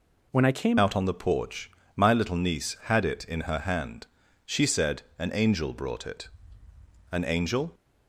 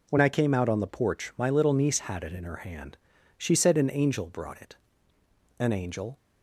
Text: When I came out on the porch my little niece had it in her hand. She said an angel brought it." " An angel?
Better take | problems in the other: second | changes voice at "out"; from 0.7 s on; 7.0 s long // pauses between "porch" and "my"; slight; at 1.6 s; 0.28 s long // pauses between "said" and "an"; slight; at 5.0 s; 0.16 s long

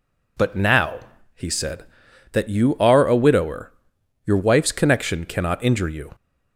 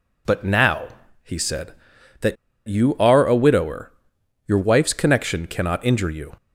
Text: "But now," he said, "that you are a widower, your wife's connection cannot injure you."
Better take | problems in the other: first | pauses between "that" and "you"; slight; at 2.3 s; 0.30 s long

